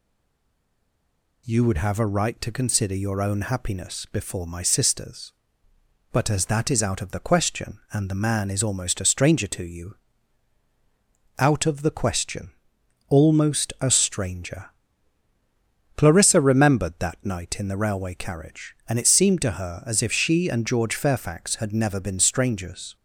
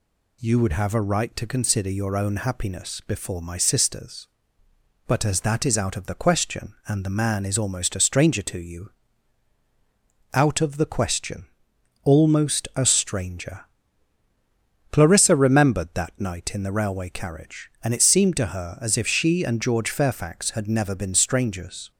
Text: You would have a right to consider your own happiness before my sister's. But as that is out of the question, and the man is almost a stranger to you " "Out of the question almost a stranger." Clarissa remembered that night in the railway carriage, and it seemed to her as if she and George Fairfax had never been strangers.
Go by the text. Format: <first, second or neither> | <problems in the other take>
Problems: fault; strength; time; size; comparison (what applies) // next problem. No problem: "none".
second | stays silent before the first word; noticeable; until 1.4 s; 1.4 s long // pauses between "question" and "almost"; noticeable; at 12.5 s; 0.58 s long; noticeable in the second